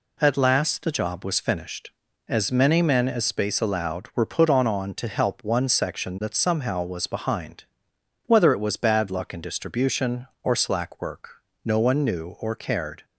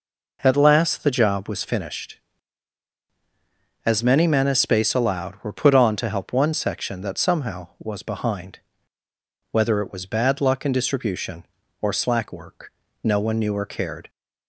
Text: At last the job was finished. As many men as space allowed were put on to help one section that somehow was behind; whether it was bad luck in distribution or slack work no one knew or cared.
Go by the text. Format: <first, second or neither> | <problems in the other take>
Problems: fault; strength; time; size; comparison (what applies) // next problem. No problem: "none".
second | says "on" twice; at 4.6 s // pauses between "work" and "no"; slight; at 11.4 s; 0.22 s long; slight in the second